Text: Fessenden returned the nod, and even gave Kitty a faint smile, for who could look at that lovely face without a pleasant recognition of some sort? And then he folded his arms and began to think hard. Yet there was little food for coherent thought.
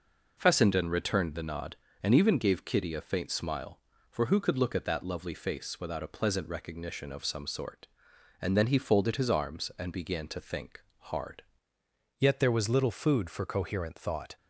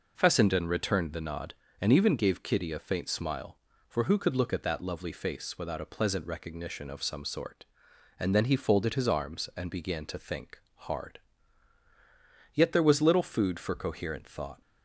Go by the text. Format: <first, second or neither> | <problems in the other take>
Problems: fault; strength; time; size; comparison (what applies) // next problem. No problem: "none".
second | pauses between "think" and "hard"; slight; at 10.8 s; 0.20 s long; slight in the second // changes voice at "Yet"; from 12.1 s on; 2.2 s long